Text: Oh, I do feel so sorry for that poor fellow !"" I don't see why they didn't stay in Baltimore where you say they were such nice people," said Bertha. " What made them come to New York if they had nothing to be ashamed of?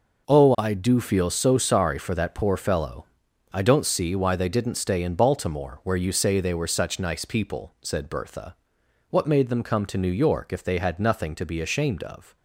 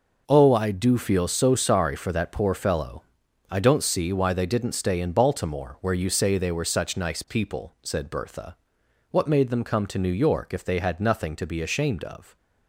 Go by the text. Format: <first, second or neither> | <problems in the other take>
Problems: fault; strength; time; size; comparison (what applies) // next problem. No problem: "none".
neither | none